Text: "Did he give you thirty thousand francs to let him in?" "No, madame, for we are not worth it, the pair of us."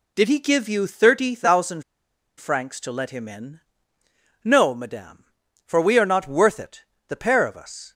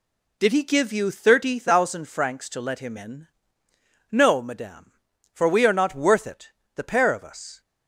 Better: second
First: pauses between "thousand" and "francs"; noticeable; at 1.8 s; 0.56 s long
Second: none

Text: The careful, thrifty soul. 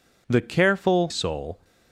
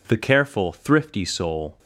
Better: second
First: skips "thrifty"; at 1.0 s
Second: none

